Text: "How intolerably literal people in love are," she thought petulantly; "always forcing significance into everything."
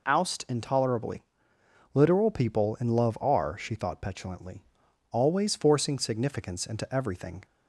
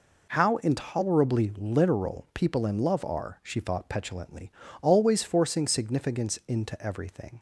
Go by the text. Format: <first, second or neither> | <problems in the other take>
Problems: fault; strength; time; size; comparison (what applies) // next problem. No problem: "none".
second | says "Oust" for "How"; at 0.0 s // pauses between "intolerably" and "literal"; noticeable; at 1.2 s; 0.72 s long